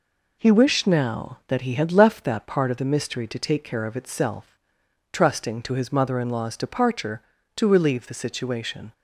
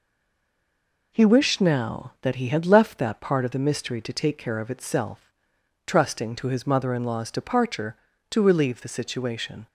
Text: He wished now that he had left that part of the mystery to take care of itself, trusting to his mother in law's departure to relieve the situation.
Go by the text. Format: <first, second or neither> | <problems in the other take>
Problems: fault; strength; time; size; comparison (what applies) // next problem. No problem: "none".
first | stays silent before the first word; until 1.1 s; 1.1 s long